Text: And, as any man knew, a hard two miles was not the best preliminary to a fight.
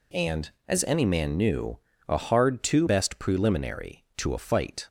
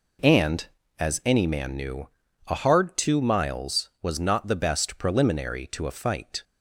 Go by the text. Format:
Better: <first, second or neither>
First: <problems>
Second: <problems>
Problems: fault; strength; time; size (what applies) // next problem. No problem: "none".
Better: second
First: skips "miles was not the"; at 2.8 s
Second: none